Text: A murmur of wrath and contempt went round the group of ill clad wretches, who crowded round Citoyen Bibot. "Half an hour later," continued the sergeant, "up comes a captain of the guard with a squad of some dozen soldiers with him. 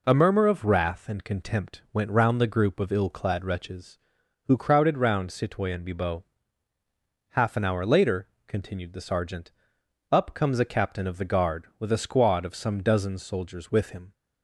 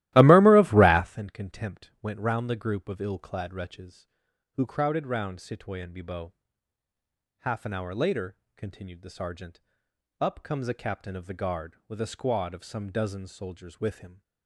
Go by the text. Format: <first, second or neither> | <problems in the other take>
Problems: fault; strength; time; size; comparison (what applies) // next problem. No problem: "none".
first | starts louder than the rest; strong; until 1.3 s; 16 dB